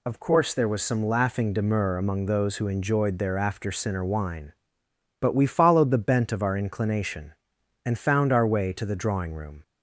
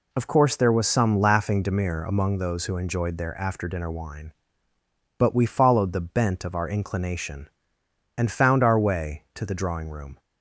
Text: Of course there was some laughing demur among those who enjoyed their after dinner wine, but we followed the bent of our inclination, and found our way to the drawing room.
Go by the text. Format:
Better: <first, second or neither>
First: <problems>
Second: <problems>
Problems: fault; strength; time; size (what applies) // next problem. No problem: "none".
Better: second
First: says "sinner" for "dinner"; at 3.7 s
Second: none